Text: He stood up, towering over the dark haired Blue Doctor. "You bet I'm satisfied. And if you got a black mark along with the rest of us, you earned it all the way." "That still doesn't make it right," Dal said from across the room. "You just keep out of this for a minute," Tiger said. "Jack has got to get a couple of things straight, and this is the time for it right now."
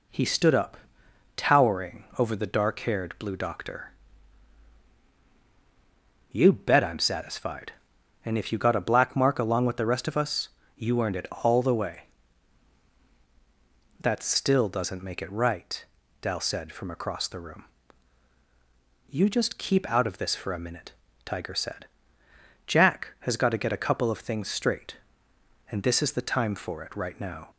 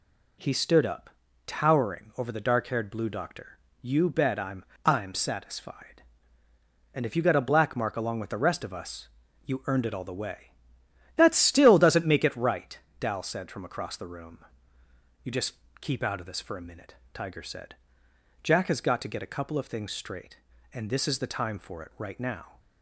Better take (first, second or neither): first